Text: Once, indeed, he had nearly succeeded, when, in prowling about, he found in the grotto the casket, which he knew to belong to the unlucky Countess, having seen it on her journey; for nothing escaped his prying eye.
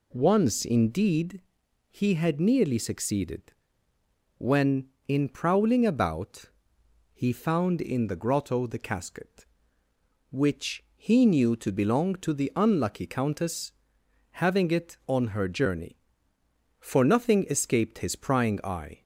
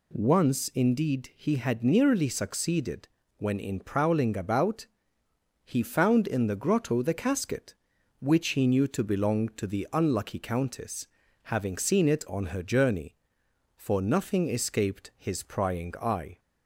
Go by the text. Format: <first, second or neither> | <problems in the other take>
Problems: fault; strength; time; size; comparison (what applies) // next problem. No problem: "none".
second | skips "seen"; at 14.7 s